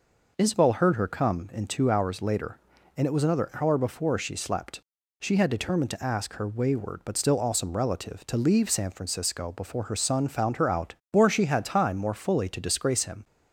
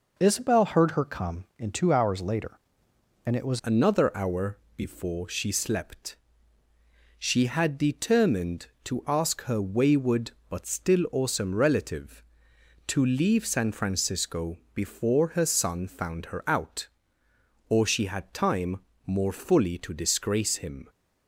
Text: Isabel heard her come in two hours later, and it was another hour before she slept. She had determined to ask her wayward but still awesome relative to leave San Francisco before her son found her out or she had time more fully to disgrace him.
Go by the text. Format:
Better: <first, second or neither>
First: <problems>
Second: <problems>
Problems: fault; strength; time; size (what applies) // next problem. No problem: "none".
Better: first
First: none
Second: changes voice at "another"; from 3.6 s on; 17.2 s long // pauses between "hour" and "before"; slight; at 4.5 s; 0.18 s long // pauses between "Francisco" and "before"; slight; at 14.5 s; 0.18 s long // pauses between "time" and "more"; slight; at 18.7 s; 0.30 s long